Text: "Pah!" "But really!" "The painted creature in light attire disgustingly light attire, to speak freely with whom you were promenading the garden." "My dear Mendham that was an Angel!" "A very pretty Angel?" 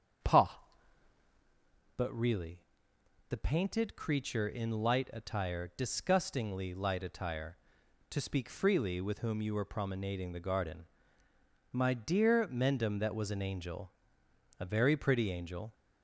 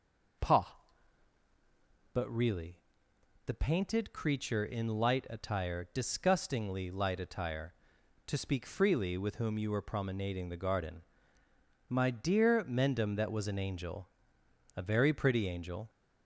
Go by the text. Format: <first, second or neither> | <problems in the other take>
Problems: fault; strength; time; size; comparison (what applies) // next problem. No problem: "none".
second | starts louder than the rest; until 1.5 s; 7 dB